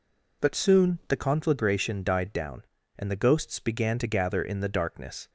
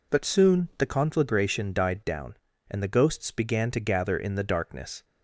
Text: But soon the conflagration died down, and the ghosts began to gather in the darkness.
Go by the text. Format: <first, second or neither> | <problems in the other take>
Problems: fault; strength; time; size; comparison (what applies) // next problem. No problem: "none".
neither | none